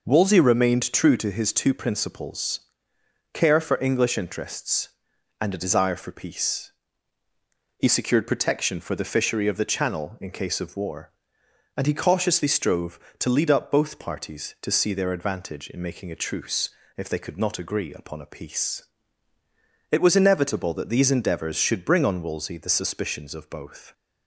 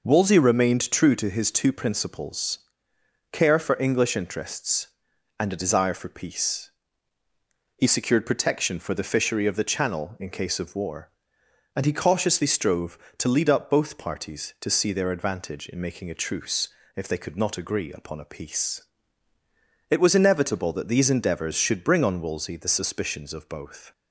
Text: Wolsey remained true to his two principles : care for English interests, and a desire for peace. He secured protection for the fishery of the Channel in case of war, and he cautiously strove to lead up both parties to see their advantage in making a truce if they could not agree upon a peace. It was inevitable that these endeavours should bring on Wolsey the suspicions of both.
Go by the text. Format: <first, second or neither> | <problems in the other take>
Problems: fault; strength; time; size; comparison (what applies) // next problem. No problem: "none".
neither | pauses between "truce" and "if"; slight; the same in both